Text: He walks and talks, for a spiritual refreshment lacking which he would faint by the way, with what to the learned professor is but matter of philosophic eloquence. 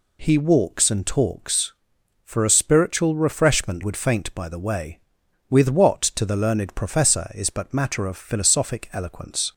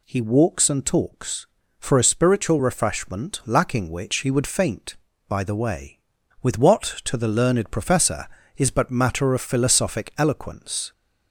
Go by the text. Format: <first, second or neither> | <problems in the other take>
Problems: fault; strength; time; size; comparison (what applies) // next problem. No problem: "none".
second | skips "lacking which he"; at 3.8 s